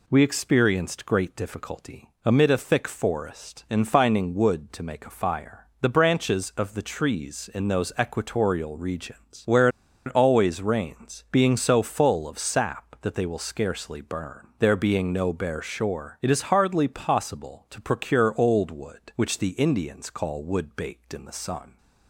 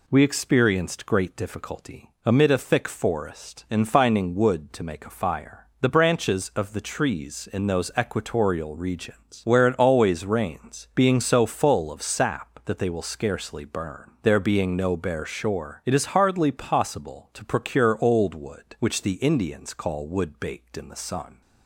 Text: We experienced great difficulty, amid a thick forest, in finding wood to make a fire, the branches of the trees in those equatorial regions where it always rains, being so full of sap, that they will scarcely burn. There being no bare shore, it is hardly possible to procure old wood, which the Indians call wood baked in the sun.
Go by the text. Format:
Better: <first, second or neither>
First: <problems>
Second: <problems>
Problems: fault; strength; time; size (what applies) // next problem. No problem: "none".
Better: second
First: pauses between "where" and "it"; at 9.6 s; 0.38 s long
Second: none